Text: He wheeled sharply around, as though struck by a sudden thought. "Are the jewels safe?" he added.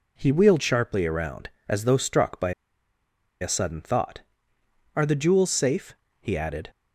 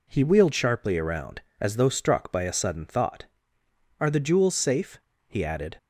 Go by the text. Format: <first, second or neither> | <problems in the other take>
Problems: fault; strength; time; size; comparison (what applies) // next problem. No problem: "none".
second | pauses between "by" and "a"; noticeable; at 2.5 s; 0.89 s long